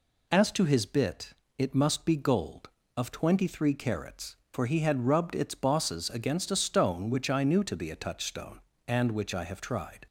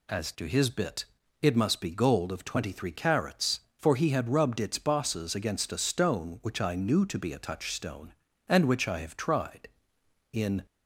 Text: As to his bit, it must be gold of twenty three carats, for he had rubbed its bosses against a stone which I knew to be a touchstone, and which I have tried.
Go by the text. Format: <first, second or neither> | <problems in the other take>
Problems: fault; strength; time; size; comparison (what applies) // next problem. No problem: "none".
first | goes on to say "In"; slight; from 10.3 s on; 0.32 s long